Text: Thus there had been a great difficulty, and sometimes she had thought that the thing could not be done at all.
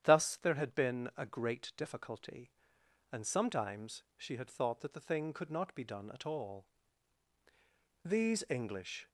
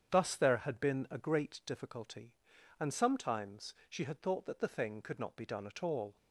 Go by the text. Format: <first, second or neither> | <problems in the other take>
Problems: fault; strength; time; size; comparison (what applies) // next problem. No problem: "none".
second | starts louder than the rest; strong; until 1.0 s; 10 dB; strong in the second // goes on to say "These English"; noticeable; from 8.0 s on; 1.0 s long